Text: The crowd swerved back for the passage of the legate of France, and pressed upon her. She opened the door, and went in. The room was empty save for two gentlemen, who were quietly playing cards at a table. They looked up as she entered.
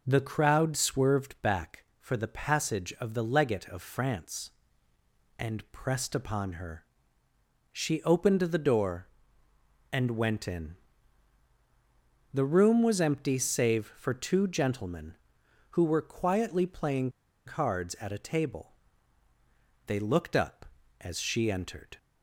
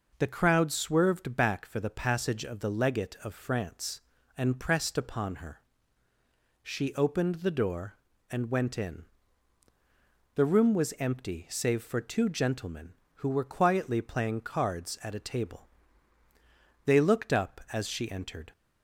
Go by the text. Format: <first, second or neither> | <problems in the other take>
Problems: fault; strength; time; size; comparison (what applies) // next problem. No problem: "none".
second | pauses between "playing" and "cards"; at 17.0 s; 0.37 s long